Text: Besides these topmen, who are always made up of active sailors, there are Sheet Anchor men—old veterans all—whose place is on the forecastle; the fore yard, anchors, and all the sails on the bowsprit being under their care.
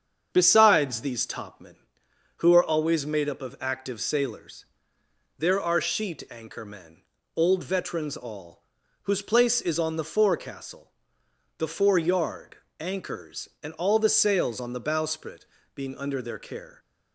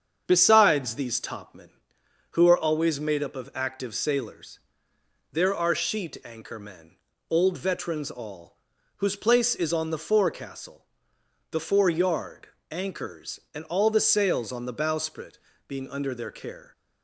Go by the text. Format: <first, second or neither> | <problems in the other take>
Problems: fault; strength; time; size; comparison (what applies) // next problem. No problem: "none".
neither | starts louder than the rest; strong; the same in both // pauses between "bowsprit" and "being"; slight; the same in both